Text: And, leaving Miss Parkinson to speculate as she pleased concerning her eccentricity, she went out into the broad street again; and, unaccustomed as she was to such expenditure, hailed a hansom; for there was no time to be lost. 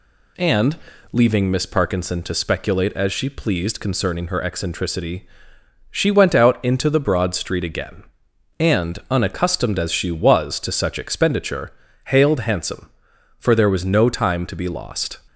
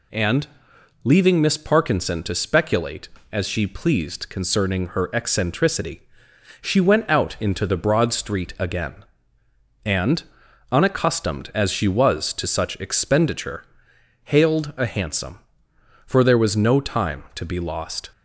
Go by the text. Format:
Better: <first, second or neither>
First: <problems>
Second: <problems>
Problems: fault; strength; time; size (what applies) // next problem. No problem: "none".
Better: second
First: skips "a"; at 12.3 s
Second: none